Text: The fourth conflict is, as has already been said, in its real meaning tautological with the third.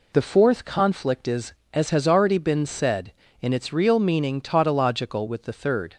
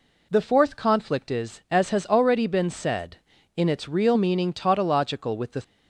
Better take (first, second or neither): first